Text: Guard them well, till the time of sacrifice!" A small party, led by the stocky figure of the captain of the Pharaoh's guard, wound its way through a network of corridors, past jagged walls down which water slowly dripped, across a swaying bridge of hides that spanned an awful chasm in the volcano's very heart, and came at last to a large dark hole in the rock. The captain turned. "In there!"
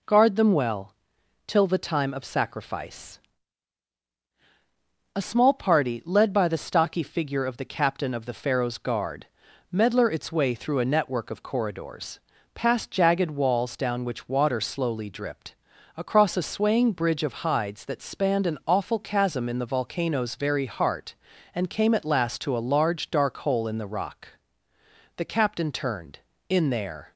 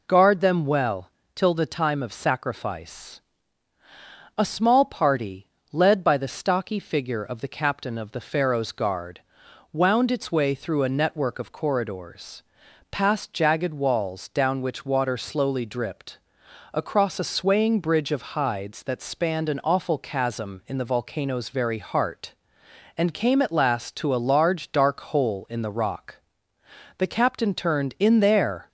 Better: second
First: says "medler" for "wound"; at 9.7 s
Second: none

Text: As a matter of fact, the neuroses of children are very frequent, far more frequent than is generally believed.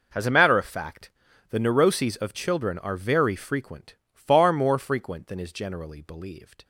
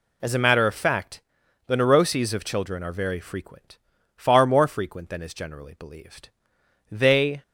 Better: first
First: none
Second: goes on to say "They"; from 6.9 s on; 0.52 s long

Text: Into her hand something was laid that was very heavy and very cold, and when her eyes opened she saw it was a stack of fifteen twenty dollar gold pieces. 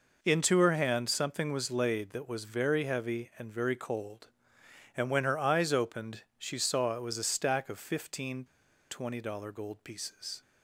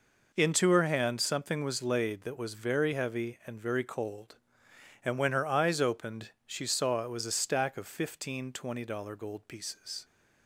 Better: second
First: pauses between "fifteen" and "twenty"; noticeable; at 8.4 s; 0.46 s long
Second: none

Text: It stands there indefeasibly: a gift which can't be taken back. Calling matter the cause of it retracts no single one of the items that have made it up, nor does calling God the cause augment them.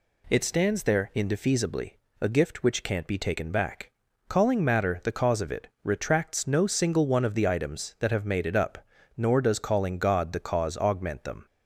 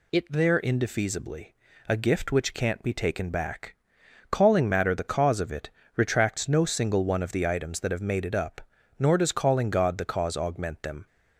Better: first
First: pauses between "it" and "retracts"; slight; at 5.6 s; 0.16 s long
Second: skips "stands"; at 0.2 s // pauses between "it" and "retracts"; slight; at 5.6 s; 0.26 s long

